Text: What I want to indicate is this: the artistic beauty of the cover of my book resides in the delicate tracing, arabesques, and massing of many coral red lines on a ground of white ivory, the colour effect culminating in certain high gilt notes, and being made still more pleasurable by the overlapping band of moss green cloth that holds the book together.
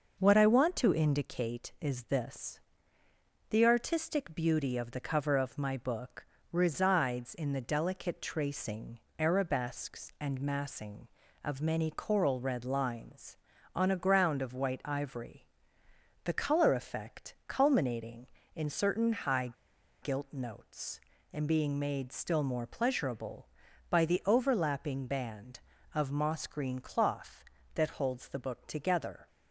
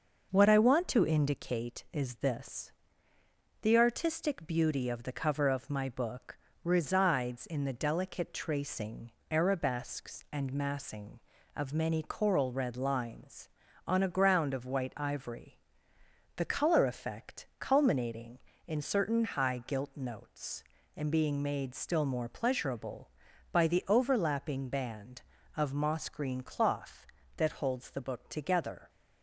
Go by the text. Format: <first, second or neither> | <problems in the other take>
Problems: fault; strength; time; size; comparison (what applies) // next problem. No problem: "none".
second | pauses between "book" and "resides"; slight; at 6.2 s; 0.26 s long; slight in the second // pauses between "high" and "gilt"; noticeable; at 19.5 s; 0.51 s long